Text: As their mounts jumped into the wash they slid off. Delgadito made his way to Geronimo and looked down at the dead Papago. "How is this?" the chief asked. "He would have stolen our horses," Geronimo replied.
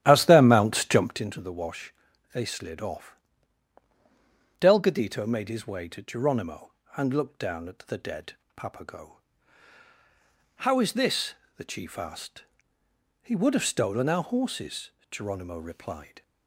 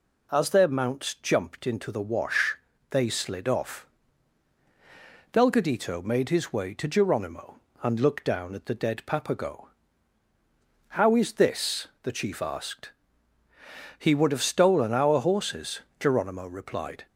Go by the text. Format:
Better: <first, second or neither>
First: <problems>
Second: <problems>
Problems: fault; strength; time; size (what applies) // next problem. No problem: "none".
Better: second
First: starts louder than the rest; strong; until 1.3 s; 12.5 dB // pauses between "wash" and "they"; at 1.9 s; 0.40 s long // pauses between "dead" and "Papago"; slight; at 8.3 s; 0.22 s long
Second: pauses between "wash" and "they"; slight; at 2.5 s; 0.34 s long